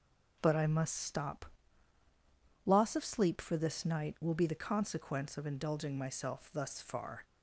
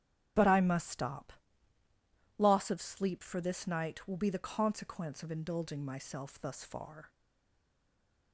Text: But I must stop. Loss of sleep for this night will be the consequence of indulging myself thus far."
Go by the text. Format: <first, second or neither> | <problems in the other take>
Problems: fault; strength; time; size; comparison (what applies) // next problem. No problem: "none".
first | starts louder than the rest; strong; until 2.4 s; 9.5 dB // stays silent after the last word; noticeable; from 7.0 s on; 1.3 s long